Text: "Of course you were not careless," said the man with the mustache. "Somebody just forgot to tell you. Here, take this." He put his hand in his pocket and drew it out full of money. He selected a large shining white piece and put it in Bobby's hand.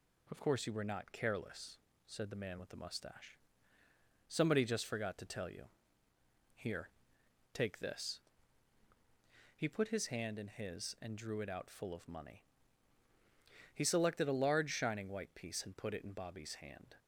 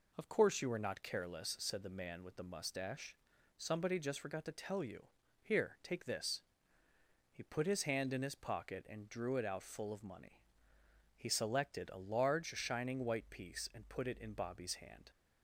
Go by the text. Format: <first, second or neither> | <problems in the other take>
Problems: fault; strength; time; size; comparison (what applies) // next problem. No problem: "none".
second | skips "pocket"; at 10.9 s